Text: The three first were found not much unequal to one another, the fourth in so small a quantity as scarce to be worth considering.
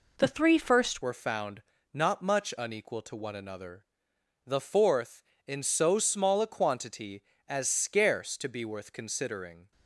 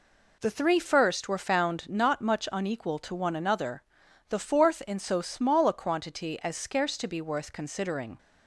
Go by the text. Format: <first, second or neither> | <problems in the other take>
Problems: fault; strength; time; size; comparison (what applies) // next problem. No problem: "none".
second | changes voice at "were"; from 1.0 s on; 8.7 s long // pauses between "found" and "not"; slight; at 1.6 s; 0.30 s long